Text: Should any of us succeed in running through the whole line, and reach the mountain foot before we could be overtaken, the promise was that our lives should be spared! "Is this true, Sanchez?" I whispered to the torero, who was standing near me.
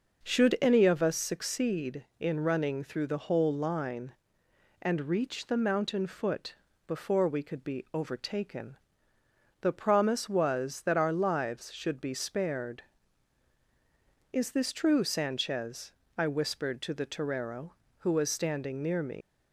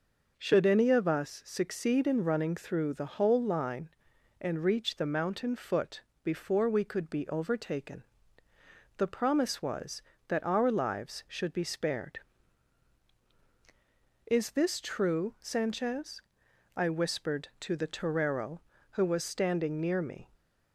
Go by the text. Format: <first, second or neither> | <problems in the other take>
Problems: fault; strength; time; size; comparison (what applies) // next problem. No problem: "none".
second | pauses between "foot" and "before"; slight; at 6.5 s; 0.32 s long; slight in the second // leaves "me" unfinished; at 19.2 s; 130 ms